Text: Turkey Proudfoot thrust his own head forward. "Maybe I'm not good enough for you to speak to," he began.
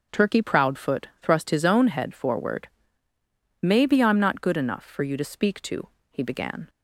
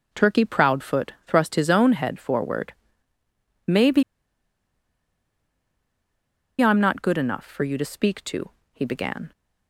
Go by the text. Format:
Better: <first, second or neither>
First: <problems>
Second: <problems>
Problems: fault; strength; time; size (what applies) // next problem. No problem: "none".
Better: first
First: starts louder than the rest; until 1.2 s; 6 dB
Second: starts louder than the rest; until 1.2 s; 6 dB // pauses between "Maybe" and "I'm"; strong; at 4.0 s; 2.5 s long